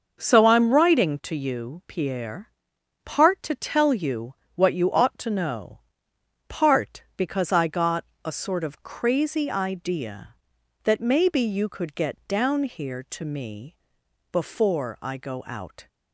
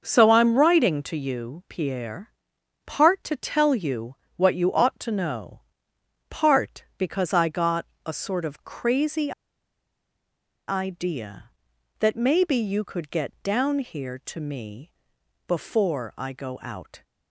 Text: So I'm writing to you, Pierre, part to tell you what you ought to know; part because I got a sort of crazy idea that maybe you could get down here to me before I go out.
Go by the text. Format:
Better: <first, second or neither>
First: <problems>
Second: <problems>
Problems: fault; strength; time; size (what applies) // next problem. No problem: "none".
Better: first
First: starts louder than the rest; until 1.2 s; 6.5 dB // pauses between "you" and "what"; slight; at 4.3 s; 0.18 s long // pauses between "got" and "a"; slight; at 8.0 s; 0.20 s long // pauses between "me" and "before"; noticeable; at 13.7 s; 0.58 s long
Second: starts louder than the rest; until 1.0 s; 6.5 dB // pauses between "you" and "what"; slight; at 4.1 s; 0.18 s long // pauses between "got" and "a"; slight; at 7.8 s; 0.20 s long // pauses between "crazy" and "idea"; strong; at 9.3 s; 1.3 s long // pauses between "me" and "before"; noticeable; at 14.8 s; 0.58 s long